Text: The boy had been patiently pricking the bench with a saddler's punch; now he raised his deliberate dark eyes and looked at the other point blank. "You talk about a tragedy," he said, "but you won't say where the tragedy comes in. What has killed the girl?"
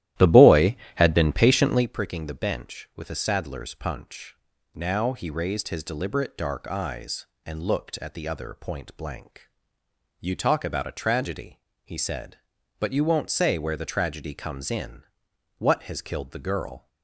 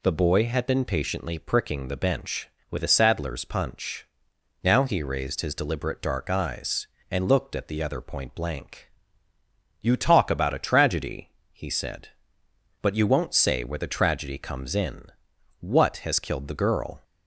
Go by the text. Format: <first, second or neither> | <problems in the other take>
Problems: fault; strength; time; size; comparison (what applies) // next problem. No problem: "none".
second | starts louder than the rest; strong; until 1.9 s; 13.5 dB